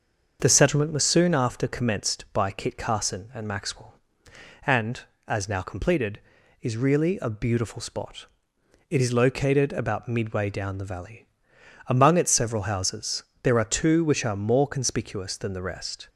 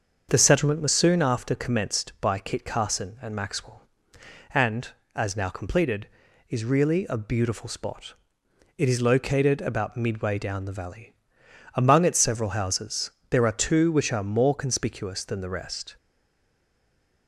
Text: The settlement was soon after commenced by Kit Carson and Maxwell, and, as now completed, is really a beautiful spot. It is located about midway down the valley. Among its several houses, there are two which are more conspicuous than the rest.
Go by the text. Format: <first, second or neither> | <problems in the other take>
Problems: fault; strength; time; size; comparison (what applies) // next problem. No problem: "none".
first | starts louder than the rest; until 1.3 s; 6.5 dB; also in the first // stays silent after the last word; noticeable; from 15.9 s on; 1.3 s long